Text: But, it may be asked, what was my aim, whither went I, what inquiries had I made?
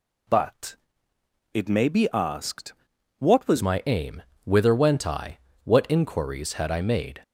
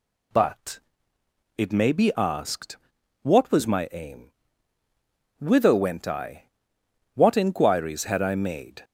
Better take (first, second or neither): second